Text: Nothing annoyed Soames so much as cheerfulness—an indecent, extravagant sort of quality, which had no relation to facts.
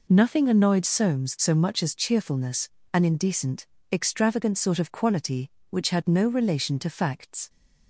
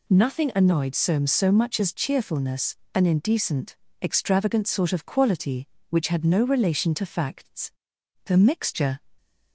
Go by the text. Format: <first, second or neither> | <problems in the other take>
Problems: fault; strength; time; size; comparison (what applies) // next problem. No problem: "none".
first | goes on to say "The mixture"; noticeable; from 8.2 s on; 0.72 s long